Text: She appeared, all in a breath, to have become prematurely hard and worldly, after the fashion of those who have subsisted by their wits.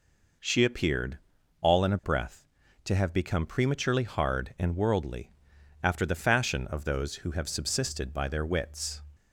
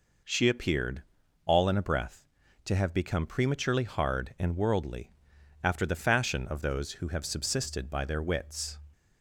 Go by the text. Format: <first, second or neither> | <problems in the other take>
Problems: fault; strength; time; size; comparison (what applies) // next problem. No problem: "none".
neither | none